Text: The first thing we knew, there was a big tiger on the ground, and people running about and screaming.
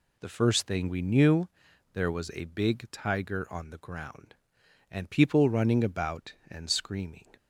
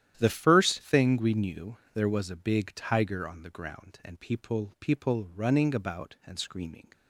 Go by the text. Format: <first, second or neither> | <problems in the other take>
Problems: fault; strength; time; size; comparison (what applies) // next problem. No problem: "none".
first | starts louder than the rest; strong; until 1.1 s; 11 dB // says "people" twice; at 4.7 s